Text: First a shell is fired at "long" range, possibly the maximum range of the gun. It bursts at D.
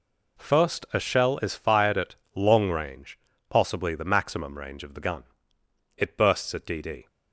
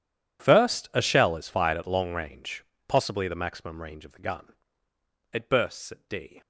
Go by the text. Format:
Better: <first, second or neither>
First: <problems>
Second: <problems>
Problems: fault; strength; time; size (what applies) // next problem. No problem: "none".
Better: second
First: pauses between "at" and "long"; slight; at 2.1 s; 0.22 s long // says "D" twice; at 6.7 s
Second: none